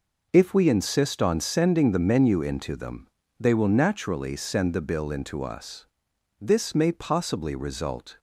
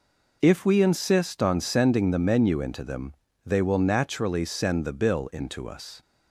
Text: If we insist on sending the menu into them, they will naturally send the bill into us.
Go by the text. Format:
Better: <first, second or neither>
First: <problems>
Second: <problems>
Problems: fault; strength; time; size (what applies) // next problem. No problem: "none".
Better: second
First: goes on to say "This may possibly result"; strong; from 6.3 s on; 1.8 s long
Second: none